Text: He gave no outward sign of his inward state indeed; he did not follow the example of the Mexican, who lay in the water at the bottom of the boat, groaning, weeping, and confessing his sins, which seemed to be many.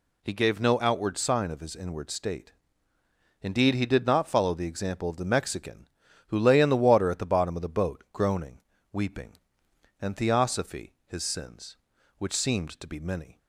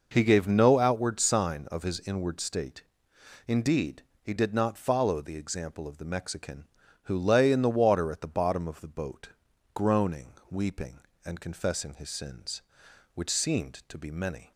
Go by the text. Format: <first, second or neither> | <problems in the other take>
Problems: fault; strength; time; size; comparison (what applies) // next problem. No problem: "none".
second | pauses between "state" and "indeed"; noticeable; at 2.5 s; 0.90 s long; noticeable in the second // says "theosophy" for "confessing"; at 10.1 s